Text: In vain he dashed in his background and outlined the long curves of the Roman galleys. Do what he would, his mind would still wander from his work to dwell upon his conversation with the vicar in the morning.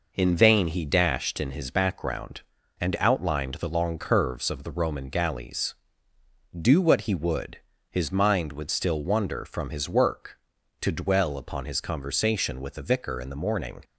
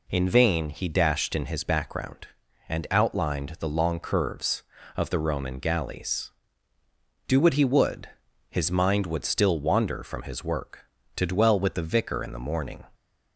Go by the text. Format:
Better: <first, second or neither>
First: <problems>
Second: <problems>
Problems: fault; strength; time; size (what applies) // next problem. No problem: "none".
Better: first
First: none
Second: skips "upon his conversation"; at 11.5 s